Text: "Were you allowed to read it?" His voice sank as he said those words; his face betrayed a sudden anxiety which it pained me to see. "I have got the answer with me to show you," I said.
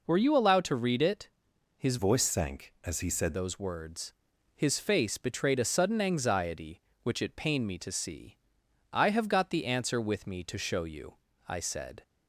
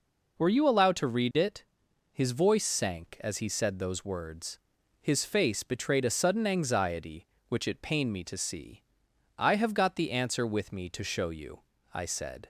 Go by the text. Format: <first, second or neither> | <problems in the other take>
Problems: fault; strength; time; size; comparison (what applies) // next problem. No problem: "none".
second | changes voice from "voice" to "said"; from 1.9 to 3.3 s; 1.4 s long